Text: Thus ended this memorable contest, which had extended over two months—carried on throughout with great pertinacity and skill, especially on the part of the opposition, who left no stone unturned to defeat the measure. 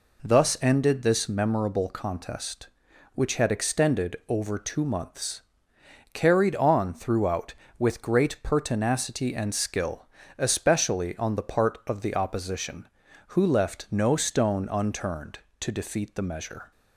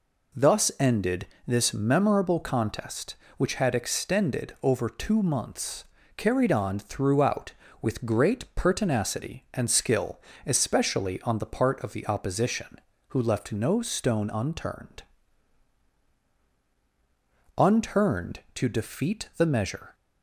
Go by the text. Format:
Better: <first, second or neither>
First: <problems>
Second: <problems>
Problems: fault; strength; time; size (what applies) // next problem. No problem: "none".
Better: first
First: none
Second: pauses between "ended" and "this"; slight; at 1.2 s; 0.20 s long // says "unturned" twice; at 17.5 s